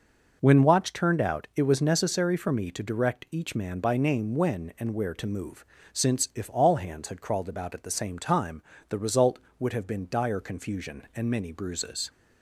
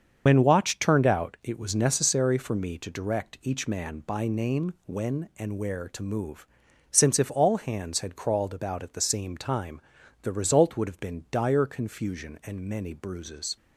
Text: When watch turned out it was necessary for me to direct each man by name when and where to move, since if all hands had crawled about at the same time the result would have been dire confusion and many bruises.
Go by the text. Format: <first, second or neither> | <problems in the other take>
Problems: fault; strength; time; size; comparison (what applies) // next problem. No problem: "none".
first | loses the start of "When"; at 0.2 s; 60 ms // starts louder than the rest; until 1.2 s; 7 dB // pauses between "time" and "the"; at 9.7 s; 0.44 s long; slight in the first